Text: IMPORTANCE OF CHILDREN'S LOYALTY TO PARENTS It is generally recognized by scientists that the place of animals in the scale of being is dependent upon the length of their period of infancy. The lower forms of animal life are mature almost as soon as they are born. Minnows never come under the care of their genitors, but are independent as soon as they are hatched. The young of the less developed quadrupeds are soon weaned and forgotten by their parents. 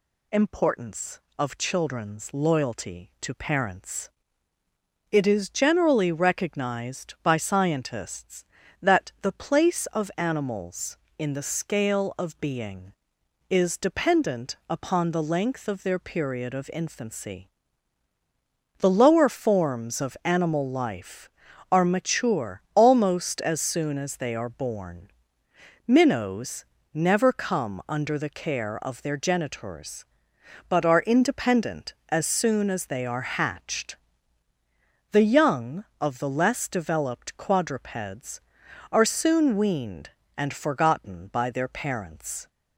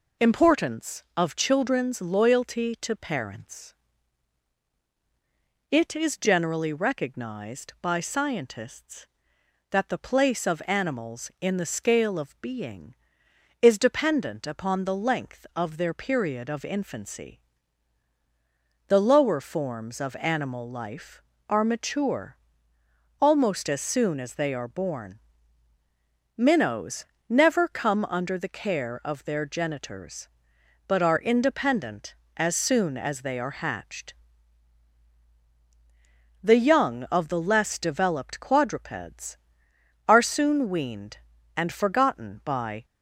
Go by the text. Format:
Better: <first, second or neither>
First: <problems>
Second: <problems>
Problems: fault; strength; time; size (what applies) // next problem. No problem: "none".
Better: first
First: pauses between "PARENTS" and "It"; at 4.0 s; 1.0 s long // pauses between "Minnows" and "never"; slight; at 26.6 s; 0.30 s long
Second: pauses between "PARENTS" and "It"; strong; at 3.7 s; 1.9 s long // pauses between "mature" and "almost"; noticeable; at 22.3 s; 0.81 s long // pauses between "Minnows" and "never"; slight; at 27.0 s; 0.22 s long // stops before "their parents"; at 42.8 s